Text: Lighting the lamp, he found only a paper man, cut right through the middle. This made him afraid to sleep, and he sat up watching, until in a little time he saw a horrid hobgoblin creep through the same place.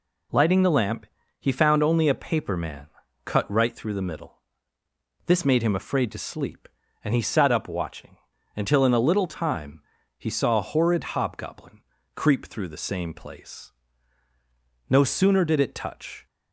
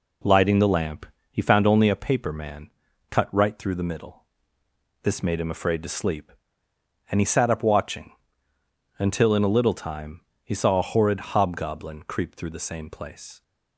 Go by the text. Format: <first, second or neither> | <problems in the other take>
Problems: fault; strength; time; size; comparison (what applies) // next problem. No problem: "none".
second | pauses between "time" and "he"; slight; at 9.8 s; 0.36 s long; slight in the second // pauses between "hobgoblin" and "creep"; slight; at 11.7 s; 0.34 s long // goes on to say "No sooner did it touch"; from 14.8 s on; 1.3 s long